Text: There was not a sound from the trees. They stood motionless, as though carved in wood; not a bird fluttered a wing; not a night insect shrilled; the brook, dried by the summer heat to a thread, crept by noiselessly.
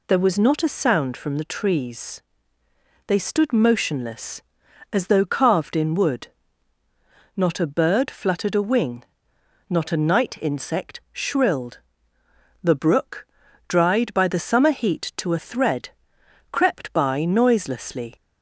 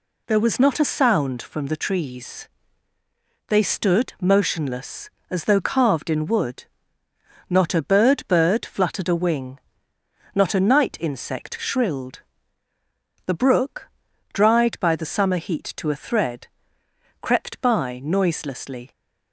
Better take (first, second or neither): first